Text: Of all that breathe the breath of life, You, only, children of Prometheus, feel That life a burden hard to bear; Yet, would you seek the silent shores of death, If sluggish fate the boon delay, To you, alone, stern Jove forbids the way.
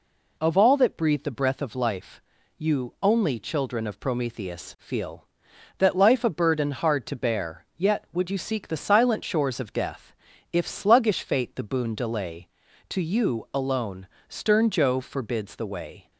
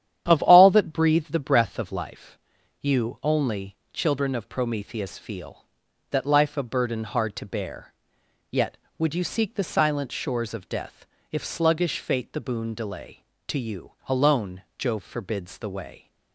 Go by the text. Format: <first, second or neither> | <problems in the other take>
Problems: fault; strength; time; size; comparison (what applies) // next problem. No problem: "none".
first | starts louder than the rest; strong; until 1.2 s; 10 dB // skips "stern"; at 14.6 s